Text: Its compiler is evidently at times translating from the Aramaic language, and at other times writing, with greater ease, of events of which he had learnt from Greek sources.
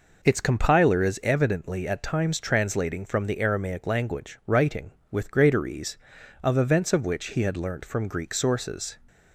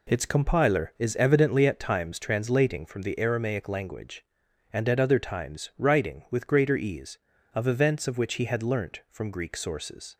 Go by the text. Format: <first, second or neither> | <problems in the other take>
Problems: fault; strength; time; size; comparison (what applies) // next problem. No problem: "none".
second | skips "and at other times"; at 4.4 s